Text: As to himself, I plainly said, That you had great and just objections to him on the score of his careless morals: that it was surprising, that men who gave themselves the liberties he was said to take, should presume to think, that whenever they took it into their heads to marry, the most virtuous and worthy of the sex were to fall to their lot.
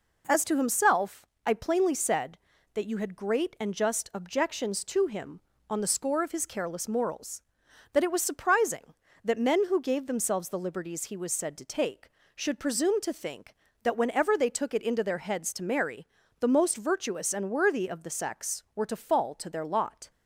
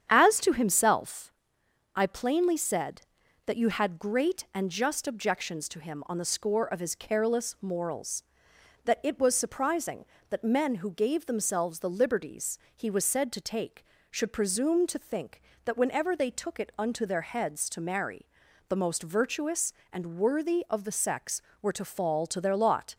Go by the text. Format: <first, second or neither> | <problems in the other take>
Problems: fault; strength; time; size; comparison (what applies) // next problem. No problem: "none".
first | starts louder than the rest; strong; until 1.1 s; 8.5 dB // pauses between "liberties" and "he"; slight; at 12.5 s; 0.16 s long // says "unto" for "into"; at 16.7 s